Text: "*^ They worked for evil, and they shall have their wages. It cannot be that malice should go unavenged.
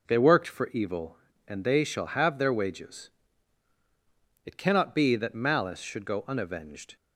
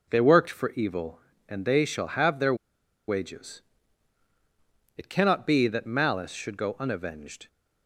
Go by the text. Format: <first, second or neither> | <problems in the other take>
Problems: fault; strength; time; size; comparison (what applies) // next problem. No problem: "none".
first | pauses between "their" and "wages"; noticeable; at 2.5 s; 0.53 s long